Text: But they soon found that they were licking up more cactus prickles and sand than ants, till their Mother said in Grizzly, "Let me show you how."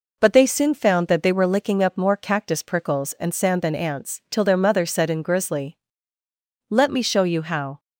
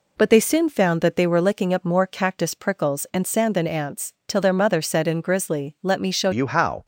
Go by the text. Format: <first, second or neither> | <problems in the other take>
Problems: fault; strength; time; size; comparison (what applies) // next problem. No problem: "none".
first | changes voice at "you"; from 6.3 s on; 0.5 s long